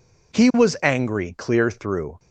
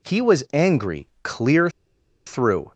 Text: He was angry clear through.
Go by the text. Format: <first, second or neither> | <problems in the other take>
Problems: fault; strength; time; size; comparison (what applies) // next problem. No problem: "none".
first | pauses between "clear" and "through"; noticeable; at 1.6 s; 0.56 s long